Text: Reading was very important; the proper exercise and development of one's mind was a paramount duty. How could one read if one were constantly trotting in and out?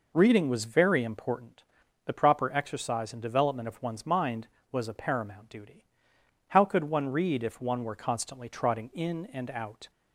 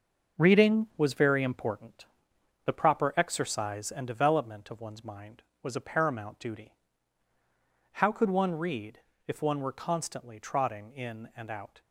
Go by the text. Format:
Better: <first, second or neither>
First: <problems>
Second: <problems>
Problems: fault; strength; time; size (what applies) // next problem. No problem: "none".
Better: first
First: none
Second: gets quieter; strong; throughout; 7.5 dB // pauses between "read" and "if"; slight; at 9.0 s; 0.26 s long